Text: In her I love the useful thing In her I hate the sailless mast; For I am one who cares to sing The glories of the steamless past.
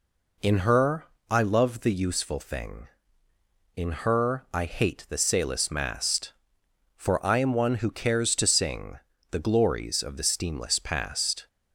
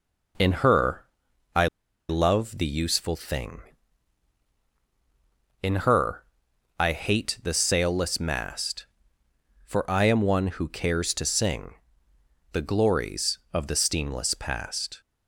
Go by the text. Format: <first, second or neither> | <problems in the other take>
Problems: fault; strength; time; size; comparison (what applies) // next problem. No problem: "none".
first | pauses between "her" and "I"; noticeable; at 1.0 s; 0.48 s long; slight in the first // pauses between "I" and "love"; at 1.6 s; 0.43 s long // pauses between "her" and "I"; noticeable; at 6.2 s; 0.54 s long // pauses between "sing" and "The"; noticeable; at 11.7 s; 0.80 s long; slight in the first